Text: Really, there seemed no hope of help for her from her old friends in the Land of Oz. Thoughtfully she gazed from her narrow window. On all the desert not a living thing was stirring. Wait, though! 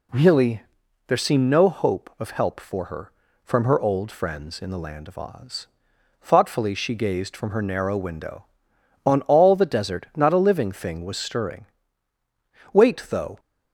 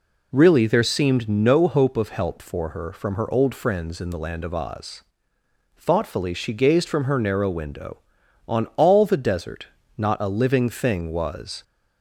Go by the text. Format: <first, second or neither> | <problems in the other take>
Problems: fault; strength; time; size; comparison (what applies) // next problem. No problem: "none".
first | pauses between "desert" and "not"; slight; at 9.6 s; 0.30 s long // stops before "stirring Wait though"; at 11.6 s